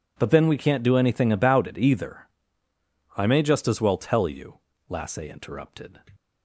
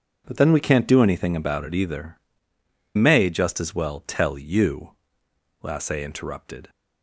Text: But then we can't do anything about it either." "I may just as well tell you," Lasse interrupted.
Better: first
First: none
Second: skips "I"; at 2.5 s

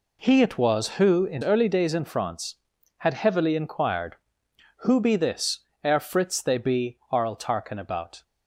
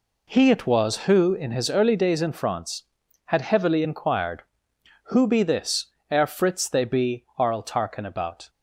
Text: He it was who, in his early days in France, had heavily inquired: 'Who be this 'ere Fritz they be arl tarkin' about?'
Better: second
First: skips "his"; at 1.4 s // pauses between "this" and "ere"; slight; at 5.5 s; 0.26 s long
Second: pauses between "this" and "ere"; slight; at 5.8 s; 0.26 s long

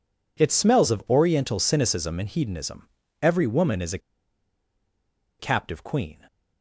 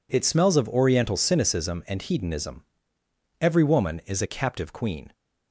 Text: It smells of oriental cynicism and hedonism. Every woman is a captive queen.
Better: second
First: pauses between "a" and "captive"; strong; at 3.9 s; 1.4 s long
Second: none

